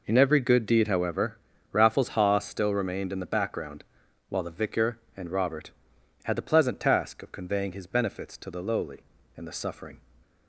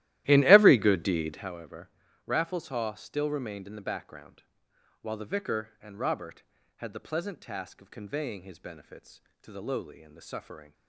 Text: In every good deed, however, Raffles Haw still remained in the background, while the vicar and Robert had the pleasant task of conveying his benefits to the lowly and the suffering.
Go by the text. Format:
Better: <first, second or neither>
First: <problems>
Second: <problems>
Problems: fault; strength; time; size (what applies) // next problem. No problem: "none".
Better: first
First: none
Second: starts louder than the rest; strong; until 1.5 s; 15 dB